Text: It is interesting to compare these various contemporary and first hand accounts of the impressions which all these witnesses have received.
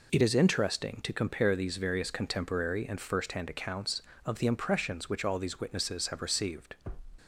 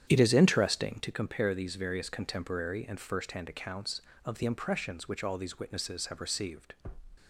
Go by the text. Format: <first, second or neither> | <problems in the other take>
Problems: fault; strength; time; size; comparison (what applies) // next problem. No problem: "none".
first | starts louder than the rest; strong; until 1.1 s; 9 dB